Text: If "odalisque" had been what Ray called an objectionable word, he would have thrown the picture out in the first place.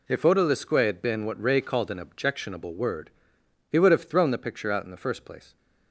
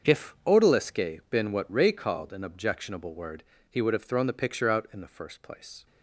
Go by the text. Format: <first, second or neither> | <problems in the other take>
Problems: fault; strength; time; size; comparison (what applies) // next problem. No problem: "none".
first | starts louder than the rest; until 1.1 s; 6.5 dB // skips "had"; at 1.2 s